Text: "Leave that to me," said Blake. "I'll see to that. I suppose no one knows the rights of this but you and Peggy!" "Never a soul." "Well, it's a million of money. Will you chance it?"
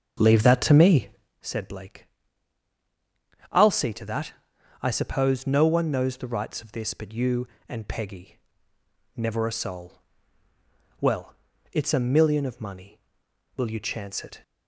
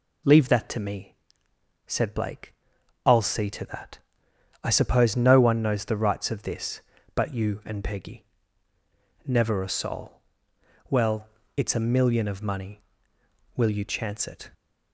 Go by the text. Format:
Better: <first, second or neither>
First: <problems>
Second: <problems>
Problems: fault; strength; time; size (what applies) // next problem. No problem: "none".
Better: second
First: starts louder than the rest; until 1.4 s; 6.5 dB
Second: none